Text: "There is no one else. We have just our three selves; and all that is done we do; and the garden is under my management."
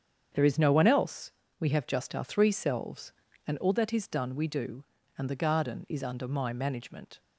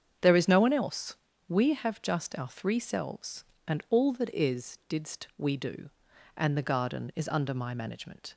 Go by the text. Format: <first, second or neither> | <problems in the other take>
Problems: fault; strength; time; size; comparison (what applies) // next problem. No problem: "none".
first | starts louder than the rest; strong; until 1.5 s; 7.5 dB; strong in the first // says "didst" for "done"; at 4.8 s